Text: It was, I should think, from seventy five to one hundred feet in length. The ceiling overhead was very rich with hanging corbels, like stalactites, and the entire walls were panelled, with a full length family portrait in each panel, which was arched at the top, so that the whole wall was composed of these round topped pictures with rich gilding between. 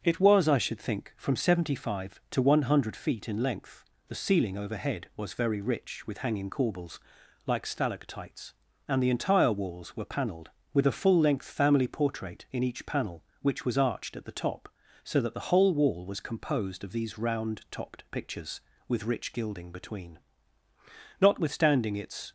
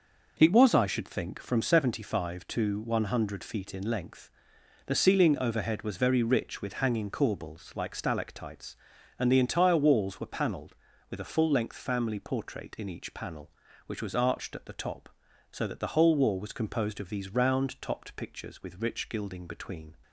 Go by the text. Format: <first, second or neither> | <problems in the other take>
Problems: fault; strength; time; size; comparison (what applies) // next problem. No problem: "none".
second | starts louder than the rest; until 1.0 s; 6.5 dB // goes on to say "Notwithstanding its"; noticeable; from 21.1 s on; 1.1 s long